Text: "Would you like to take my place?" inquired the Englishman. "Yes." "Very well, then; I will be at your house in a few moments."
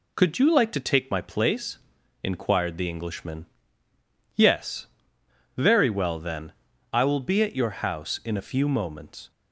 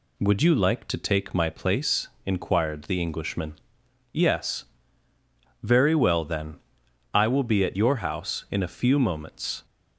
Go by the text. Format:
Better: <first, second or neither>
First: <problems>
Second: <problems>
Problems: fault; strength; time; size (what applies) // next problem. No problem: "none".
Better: second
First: says "Could" for "Would"; at 0.1 s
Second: none